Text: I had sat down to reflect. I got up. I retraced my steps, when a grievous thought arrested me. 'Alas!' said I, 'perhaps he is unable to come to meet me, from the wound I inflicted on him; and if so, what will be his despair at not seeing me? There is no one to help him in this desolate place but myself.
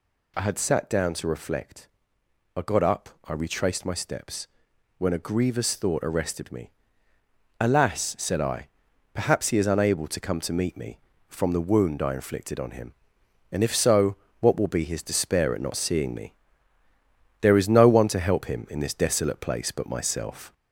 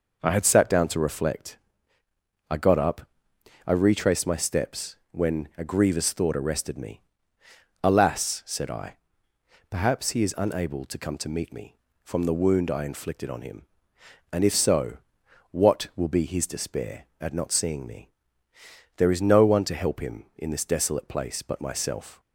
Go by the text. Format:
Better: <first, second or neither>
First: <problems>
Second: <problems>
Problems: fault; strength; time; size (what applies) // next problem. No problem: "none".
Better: second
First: gets louder; slight; throughout; 2.5 dB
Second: none